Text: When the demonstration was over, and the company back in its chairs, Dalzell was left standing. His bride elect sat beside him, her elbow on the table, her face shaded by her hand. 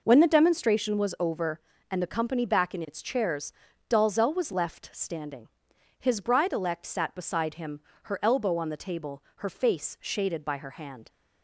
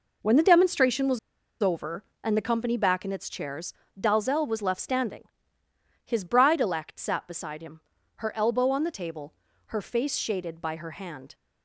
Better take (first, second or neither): first